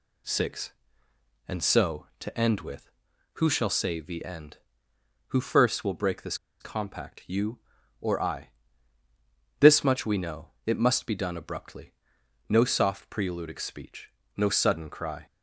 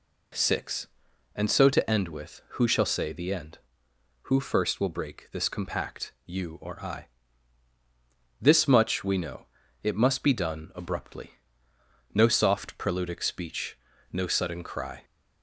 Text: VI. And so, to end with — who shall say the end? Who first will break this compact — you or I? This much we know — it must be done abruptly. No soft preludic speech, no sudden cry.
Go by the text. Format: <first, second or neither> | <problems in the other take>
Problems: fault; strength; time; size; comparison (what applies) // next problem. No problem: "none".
second | pauses between "this" and "compact"; slight; at 6.3 s; 0.24 s long